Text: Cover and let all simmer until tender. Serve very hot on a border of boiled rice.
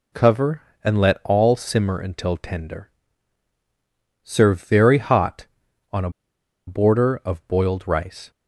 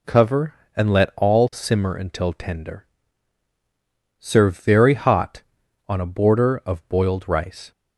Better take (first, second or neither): second